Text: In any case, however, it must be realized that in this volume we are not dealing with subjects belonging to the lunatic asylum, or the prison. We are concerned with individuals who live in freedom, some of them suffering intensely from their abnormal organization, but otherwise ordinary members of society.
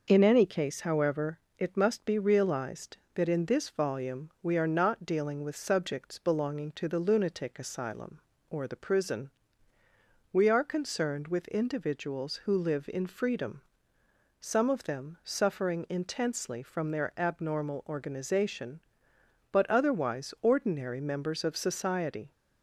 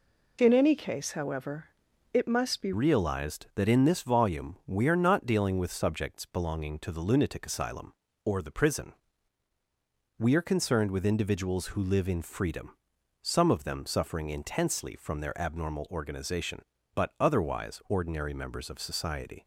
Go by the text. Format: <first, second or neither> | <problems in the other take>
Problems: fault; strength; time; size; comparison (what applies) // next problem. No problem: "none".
first | changes voice at "realized"; from 2.7 s on; 16.7 s long